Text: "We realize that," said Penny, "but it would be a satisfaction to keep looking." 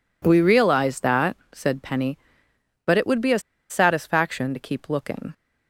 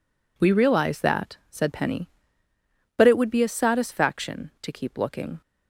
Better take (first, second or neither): second